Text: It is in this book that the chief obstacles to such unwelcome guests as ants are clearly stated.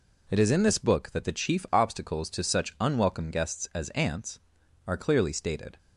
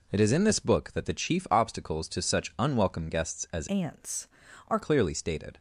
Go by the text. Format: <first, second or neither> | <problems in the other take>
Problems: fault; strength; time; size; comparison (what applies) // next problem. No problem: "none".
first | changes voice from "ants" to "are"; from 3.6 to 4.7 s; 1.1 s long